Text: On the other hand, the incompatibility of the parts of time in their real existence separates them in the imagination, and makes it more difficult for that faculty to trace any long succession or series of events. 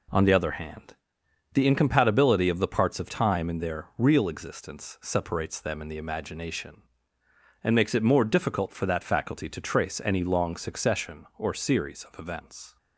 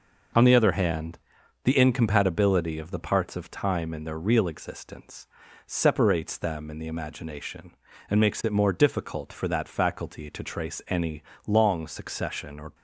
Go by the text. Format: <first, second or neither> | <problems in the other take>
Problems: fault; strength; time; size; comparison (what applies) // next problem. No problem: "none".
first | pauses between "existence" and "separates"; at 5.2 s; 0.40 s long // pauses between "any" and "long"; slight; at 11.2 s; 0.24 s long // stops before "series of events"; at 12.7 s